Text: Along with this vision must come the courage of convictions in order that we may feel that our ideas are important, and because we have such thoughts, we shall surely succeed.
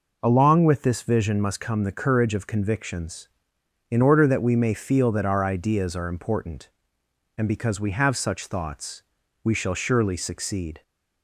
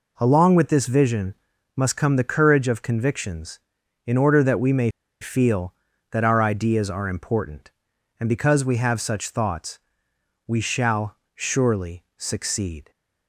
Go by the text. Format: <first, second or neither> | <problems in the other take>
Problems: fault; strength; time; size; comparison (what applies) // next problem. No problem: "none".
first | pauses between "vision" and "must"; at 1.3 s; 0.42 s long // pauses between "may" and "feel"; slight; at 4.8 s; 0.32 s long // pauses between "shall" and "surely"; slight; at 11.1 s; 0.18 s long